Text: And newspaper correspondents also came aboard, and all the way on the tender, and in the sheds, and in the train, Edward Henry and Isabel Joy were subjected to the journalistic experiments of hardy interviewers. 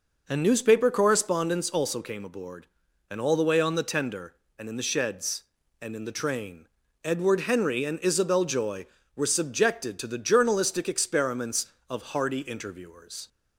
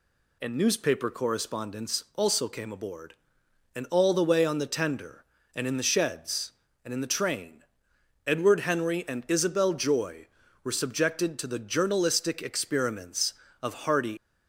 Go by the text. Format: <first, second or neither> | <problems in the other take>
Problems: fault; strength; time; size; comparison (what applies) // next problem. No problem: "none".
first | stops before "interviewers"; at 14.1 s